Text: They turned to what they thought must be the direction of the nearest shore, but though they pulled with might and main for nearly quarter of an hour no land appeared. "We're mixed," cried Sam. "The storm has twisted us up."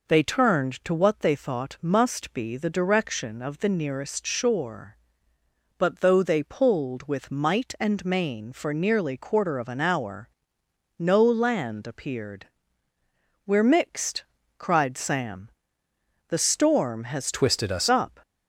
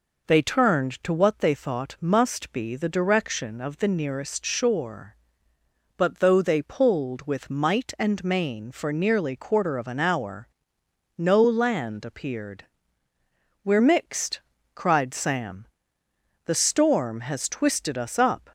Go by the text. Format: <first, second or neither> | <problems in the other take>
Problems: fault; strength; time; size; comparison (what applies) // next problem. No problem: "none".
second | pauses between "hour" and "no"; noticeable; at 10.2 s; 0.70 s long; noticeable in the second // changes voice from "twisted" to "us"; from 17.3 to 17.8 s; 0.5 s long